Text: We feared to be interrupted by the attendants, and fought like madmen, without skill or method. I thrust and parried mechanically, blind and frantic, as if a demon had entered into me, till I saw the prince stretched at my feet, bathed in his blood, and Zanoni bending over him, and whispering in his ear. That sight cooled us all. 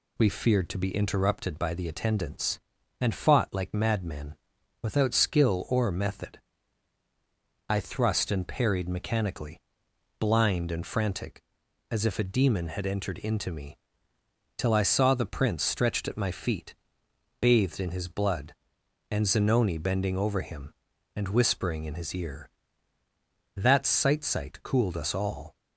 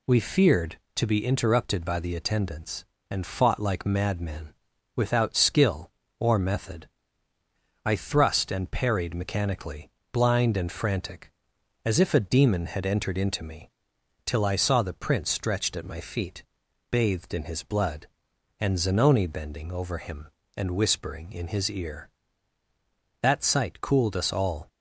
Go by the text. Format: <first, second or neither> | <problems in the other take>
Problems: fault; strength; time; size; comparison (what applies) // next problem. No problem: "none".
second | says "sight" twice; at 24.2 s